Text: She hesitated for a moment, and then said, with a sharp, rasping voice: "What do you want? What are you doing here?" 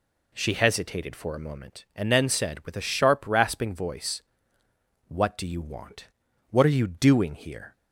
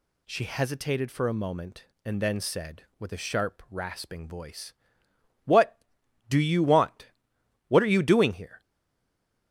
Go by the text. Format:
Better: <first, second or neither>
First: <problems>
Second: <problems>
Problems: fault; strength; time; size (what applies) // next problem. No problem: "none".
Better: first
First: none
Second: stays silent after the last word; slight; from 8.6 s on; 0.9 s long